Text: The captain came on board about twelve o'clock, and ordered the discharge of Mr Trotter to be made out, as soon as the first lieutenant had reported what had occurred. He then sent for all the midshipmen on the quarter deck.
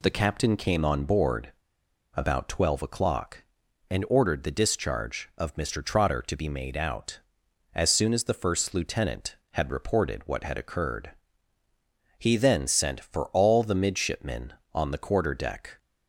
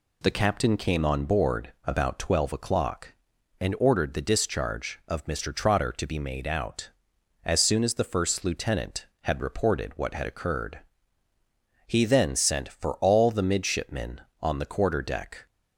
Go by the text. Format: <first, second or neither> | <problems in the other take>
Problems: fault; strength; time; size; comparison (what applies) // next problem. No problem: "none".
second | pauses between "board" and "about"; noticeable; at 1.5 s; 0.62 s long